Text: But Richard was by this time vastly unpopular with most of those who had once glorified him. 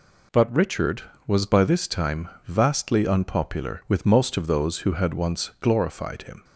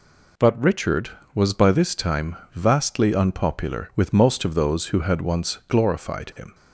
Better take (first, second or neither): neither